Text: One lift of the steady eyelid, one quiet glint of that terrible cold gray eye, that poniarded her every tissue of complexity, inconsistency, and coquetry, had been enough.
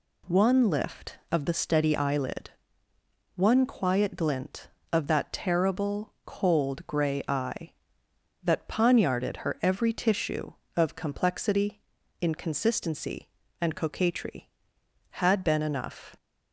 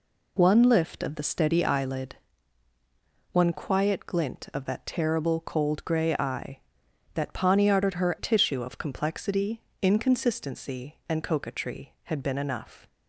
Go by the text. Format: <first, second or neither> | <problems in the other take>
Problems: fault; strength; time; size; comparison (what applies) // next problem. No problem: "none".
first | skips "every"; at 8.1 s